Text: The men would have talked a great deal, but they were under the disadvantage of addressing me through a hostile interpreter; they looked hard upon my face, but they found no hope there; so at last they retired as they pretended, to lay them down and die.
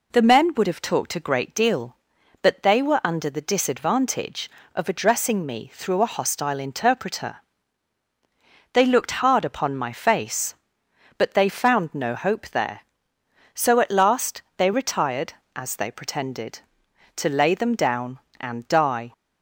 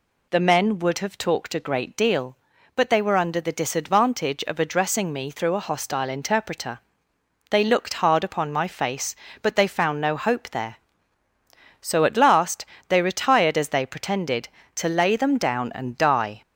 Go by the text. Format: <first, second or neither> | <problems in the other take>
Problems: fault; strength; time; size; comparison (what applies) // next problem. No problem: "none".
neither | pauses between "last" and "they"; slight; the same in both